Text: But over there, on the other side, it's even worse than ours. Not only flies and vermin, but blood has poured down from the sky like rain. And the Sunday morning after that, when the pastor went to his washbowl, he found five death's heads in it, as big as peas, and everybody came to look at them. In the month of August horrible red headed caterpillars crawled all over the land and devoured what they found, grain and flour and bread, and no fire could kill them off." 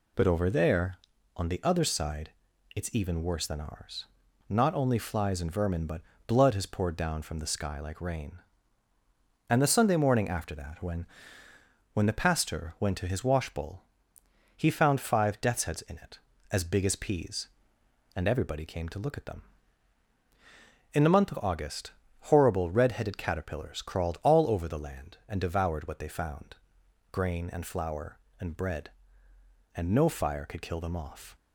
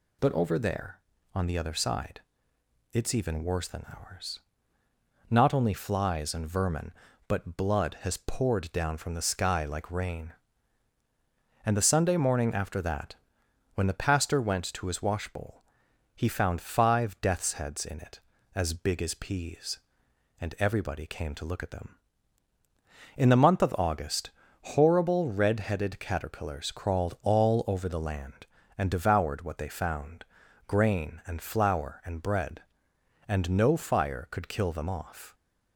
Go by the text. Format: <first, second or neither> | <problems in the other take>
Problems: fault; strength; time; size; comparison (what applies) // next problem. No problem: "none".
second | pauses between "but" and "blood"; slight; at 6.0 s; 0.26 s long // says "when" twice; at 11.9 s // pauses between "August" and "horrible"; slight; at 21.9 s; 0.36 s long; slight in the second